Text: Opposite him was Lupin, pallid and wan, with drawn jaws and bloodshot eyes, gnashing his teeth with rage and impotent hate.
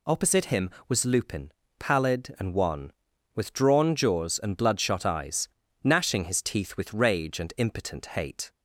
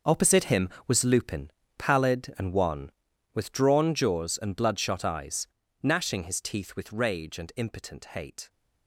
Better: first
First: none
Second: gets quieter; strong; throughout; 13.5 dB

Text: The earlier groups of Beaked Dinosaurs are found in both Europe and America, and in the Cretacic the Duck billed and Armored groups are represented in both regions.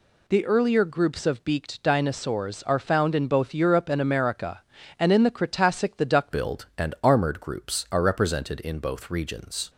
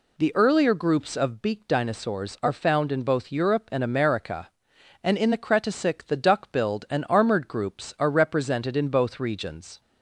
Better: second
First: changes voice at "billed"; from 6.3 s on; 3.3 s long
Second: none

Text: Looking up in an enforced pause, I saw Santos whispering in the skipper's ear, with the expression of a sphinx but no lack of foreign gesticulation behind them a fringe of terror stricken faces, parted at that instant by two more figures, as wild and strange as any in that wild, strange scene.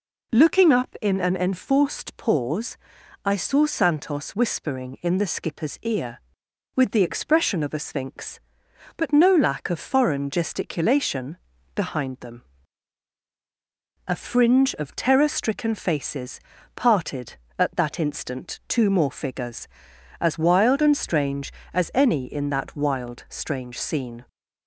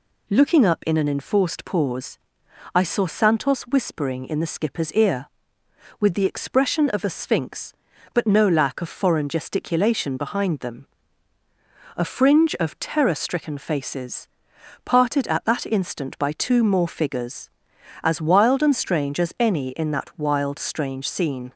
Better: second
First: pauses between "gesticulation" and "behind"; at 11.3 s; 0.38 s long // pauses between "them" and "a"; strong; at 12.4 s; 1.6 s long // skips "by"; at 18.6 s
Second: pauses between "them" and "a"; at 10.8 s; 1.1 s long

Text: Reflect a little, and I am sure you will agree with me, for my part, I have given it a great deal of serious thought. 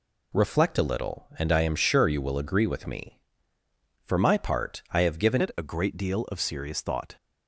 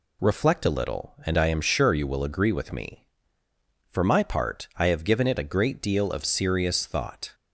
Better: second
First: changes voice at "it"; from 5.3 s on; 1.8 s long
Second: none

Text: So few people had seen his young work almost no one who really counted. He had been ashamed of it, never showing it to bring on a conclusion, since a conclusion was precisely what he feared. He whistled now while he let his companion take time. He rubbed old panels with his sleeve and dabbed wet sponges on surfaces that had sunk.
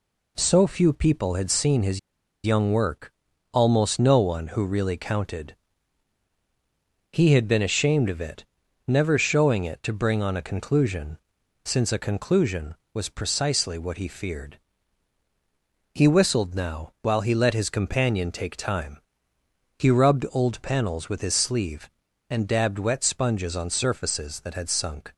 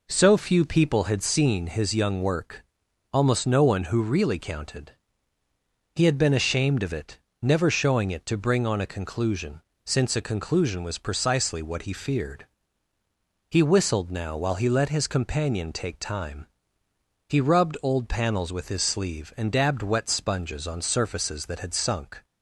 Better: second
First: pauses between "his" and "young"; noticeable; at 1.9 s; 0.46 s long // pauses between "work" and "almost"; at 3.1 s; 0.40 s long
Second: pauses between "work" and "almost"; noticeable; at 2.6 s; 0.50 s long

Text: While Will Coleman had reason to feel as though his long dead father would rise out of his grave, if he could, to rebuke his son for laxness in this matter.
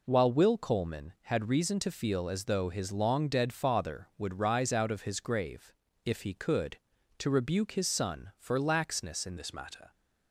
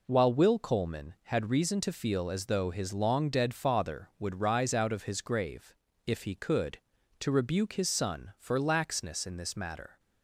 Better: second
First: changes voice at "this"; from 9.3 s on; 0.6 s long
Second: none

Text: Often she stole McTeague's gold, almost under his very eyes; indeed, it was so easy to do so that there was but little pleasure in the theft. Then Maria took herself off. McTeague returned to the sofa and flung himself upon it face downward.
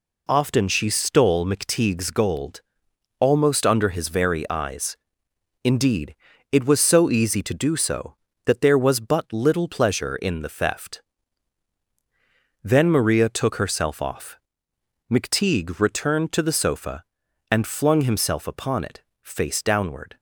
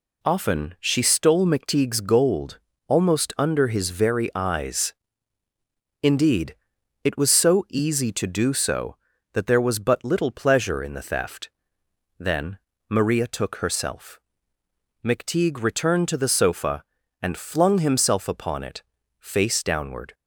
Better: first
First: pauses between "it" and "face"; slight; at 19.0 s; 0.22 s long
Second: pauses between "Then" and "Maria"; slight; at 12.5 s; 0.32 s long // skips "off"; at 14.6 s // pauses between "it" and "face"; at 18.8 s; 0.38 s long

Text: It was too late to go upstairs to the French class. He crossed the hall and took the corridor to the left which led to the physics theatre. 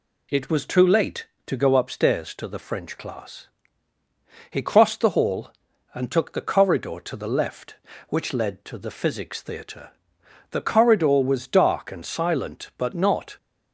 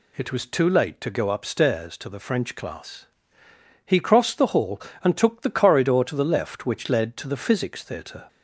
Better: second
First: goes on to say "The corridor was dark and silent but not"; strong; from 10.5 s on; 2.8 s long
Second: none

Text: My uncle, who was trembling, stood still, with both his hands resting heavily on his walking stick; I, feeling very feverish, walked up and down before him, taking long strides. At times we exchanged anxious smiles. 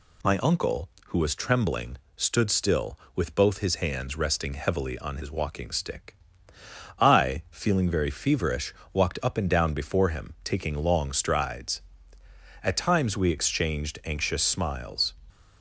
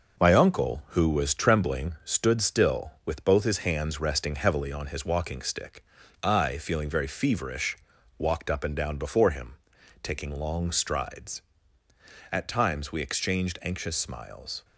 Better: first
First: none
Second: gets quieter; noticeable; throughout; 5.5 dB

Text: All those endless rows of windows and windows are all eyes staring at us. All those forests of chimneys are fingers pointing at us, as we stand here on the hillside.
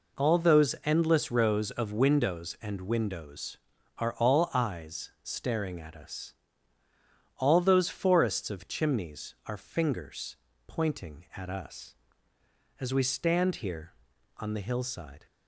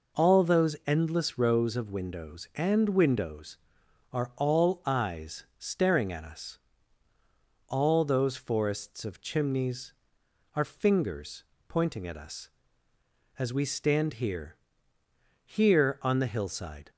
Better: first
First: pauses between "fingers" and "pointing"; slight; at 10.3 s; 0.32 s long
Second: pauses between "fingers" and "pointing"; slight; at 11.4 s; 0.24 s long // says "here" twice; at 15.4 s

